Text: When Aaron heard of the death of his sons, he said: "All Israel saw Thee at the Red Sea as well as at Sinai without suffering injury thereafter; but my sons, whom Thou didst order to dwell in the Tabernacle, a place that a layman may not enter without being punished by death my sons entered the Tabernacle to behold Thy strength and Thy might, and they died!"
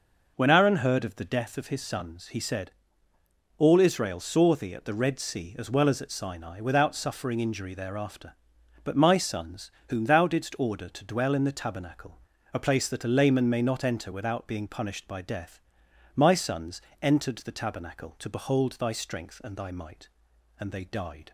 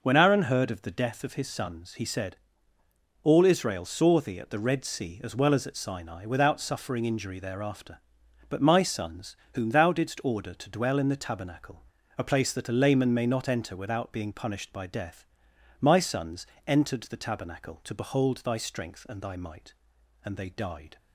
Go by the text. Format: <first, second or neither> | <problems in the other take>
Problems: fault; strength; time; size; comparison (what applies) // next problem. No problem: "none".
neither | pauses between "death" and "my"; noticeable; the same in both // pauses between "sons" and "entered"; slight; the same in both